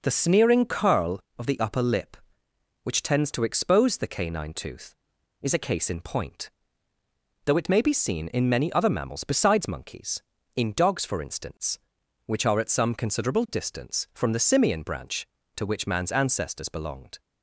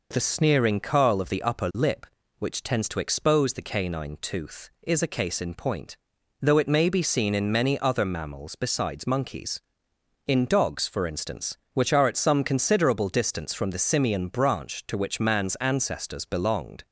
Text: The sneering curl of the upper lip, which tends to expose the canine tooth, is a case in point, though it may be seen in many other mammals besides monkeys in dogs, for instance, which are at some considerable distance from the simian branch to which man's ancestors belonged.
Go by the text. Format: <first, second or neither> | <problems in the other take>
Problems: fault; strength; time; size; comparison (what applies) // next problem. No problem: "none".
neither | none